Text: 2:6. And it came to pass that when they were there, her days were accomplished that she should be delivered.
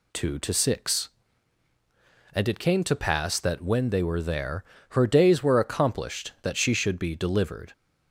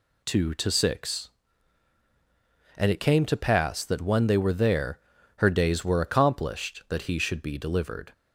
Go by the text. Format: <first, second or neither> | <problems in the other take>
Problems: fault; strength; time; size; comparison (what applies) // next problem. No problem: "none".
first | says "he" for "she"; at 7.0 s